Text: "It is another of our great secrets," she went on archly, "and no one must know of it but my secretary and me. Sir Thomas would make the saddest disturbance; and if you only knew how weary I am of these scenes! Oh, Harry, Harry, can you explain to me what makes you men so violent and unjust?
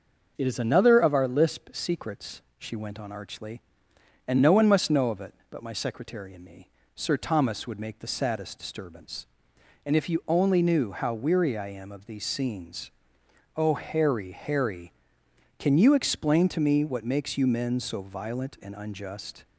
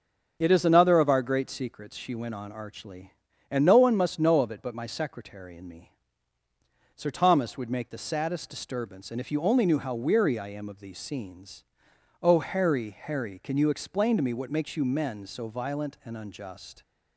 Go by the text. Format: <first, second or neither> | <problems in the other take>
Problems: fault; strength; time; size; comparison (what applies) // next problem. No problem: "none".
second | starts louder than the rest; until 1.3 s; 6 dB; also in the second // says "lisp" for "great"; at 1.2 s